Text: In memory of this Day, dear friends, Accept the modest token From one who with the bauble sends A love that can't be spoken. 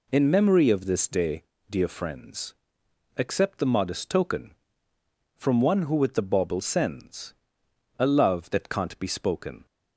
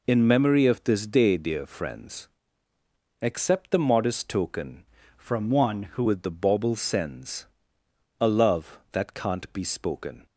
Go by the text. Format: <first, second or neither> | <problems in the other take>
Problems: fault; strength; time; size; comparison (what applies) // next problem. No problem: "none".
first | changes voice from "From" to "who"; from 5.1 to 6.0 s; 0.9 s long // pauses between "sends" and "A"; noticeable; at 7.4 s; 0.74 s long; noticeable in the first